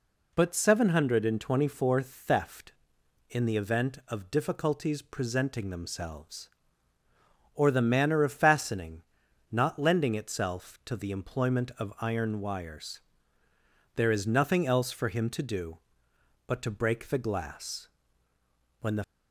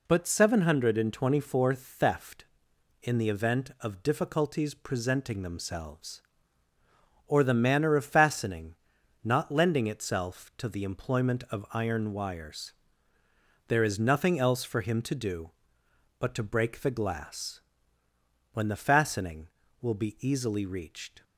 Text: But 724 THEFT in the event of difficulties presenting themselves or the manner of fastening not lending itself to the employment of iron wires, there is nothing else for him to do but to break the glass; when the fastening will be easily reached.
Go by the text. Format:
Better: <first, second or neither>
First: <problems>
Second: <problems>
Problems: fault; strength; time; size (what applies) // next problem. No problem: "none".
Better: second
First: pauses between "fastening" and "not"; noticeable; at 9.0 s; 0.48 s long // stops before "fastening will be easily reached"; at 19.0 s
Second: pauses between "fastening" and "not"; noticeable; at 8.7 s; 0.48 s long